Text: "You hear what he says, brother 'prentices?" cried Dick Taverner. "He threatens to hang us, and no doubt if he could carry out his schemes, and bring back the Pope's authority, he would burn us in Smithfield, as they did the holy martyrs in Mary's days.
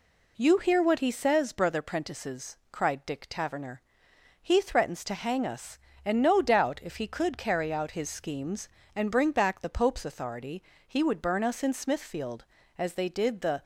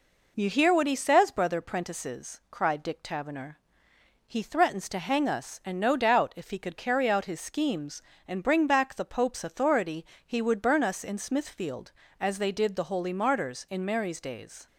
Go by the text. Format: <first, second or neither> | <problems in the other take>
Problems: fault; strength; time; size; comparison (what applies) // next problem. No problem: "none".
second | stops before "holy martyrs in Mary's days"; at 13.6 s